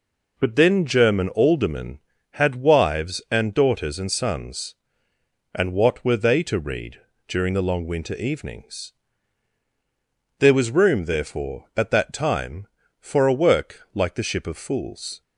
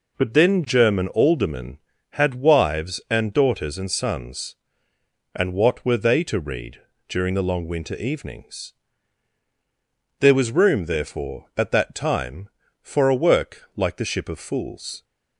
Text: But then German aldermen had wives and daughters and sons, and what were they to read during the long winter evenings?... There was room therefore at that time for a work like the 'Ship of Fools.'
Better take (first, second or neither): neither